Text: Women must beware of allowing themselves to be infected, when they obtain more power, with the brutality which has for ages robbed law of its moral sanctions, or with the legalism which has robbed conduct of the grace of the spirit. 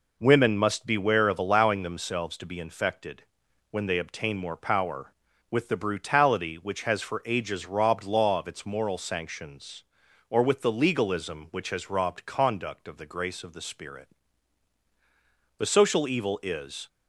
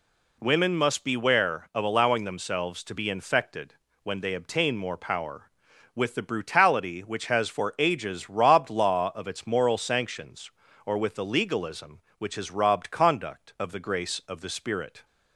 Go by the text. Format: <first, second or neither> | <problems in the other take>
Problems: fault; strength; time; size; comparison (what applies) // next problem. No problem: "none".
second | goes on to say "The social evil is"; noticeable; from 15.5 s on; 1.3 s long